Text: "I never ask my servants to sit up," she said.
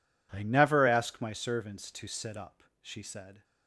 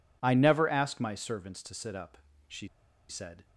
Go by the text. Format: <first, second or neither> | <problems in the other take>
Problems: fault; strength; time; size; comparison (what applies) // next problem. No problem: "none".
first | pauses between "she" and "said"; at 2.6 s; 0.41 s long